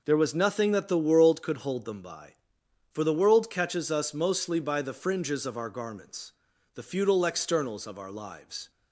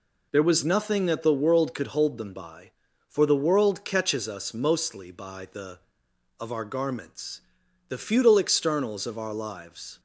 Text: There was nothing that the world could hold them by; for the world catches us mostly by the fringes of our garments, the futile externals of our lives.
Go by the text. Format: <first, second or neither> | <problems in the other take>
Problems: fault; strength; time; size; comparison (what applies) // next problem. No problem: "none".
first | skips "fringes"; at 6.0 s